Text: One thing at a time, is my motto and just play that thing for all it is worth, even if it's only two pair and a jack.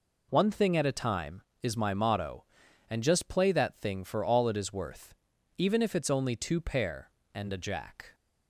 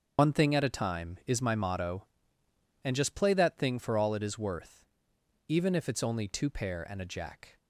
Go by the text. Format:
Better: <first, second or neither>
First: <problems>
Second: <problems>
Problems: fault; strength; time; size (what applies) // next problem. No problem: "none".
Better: first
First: none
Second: loses the start of "One"; at 0.1 s; 95 ms // starts louder than the rest; until 1.2 s; 7 dB